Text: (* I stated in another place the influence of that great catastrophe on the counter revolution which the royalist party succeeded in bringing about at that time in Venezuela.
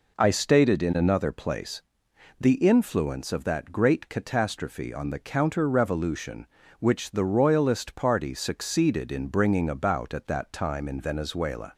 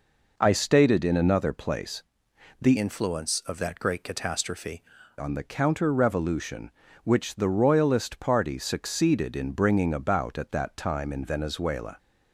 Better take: first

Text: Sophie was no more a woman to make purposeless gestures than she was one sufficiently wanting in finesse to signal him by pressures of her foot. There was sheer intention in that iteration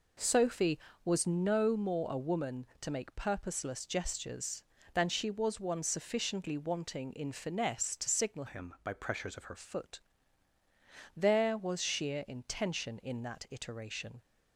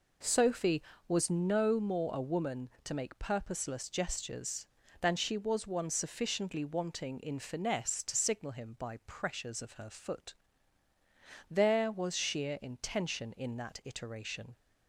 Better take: second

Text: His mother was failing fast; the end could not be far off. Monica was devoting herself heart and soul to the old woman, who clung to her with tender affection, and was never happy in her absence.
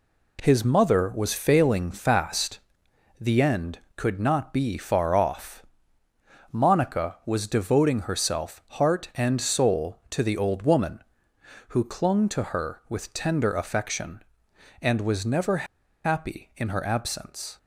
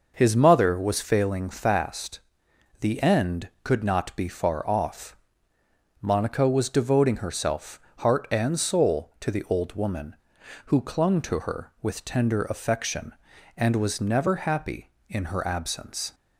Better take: second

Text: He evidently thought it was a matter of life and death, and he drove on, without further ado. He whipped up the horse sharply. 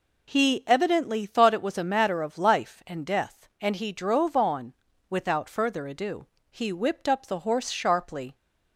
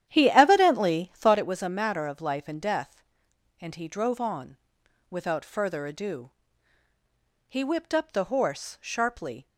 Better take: first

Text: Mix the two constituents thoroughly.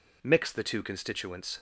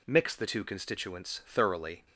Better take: second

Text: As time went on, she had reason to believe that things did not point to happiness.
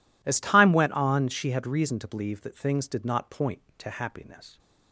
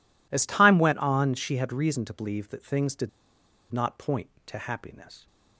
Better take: first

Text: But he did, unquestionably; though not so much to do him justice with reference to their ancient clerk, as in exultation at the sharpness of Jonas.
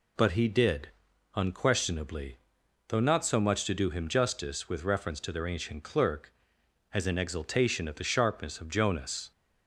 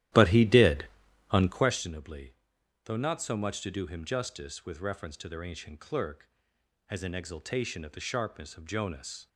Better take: first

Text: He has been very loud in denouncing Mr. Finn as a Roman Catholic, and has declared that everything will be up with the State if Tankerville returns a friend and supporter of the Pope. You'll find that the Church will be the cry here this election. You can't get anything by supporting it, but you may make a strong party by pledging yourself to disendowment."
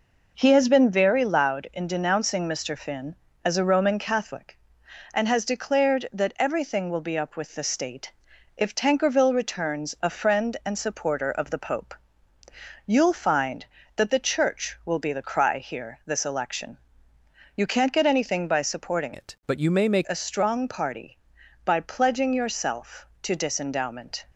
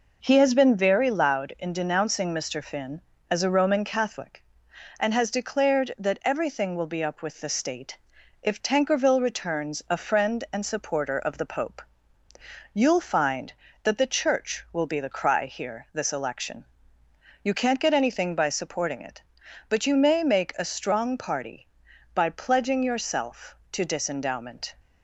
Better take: second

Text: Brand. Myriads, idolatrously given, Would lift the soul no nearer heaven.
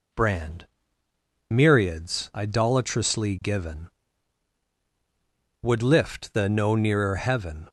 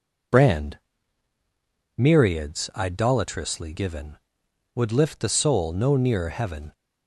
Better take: second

